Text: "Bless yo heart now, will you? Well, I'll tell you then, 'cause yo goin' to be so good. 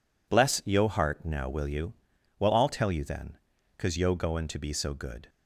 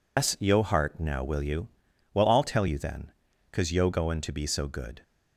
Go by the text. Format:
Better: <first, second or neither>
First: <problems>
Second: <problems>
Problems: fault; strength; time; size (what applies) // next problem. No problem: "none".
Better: first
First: none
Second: loses the start of "Bless"; at 0.1 s; 120 ms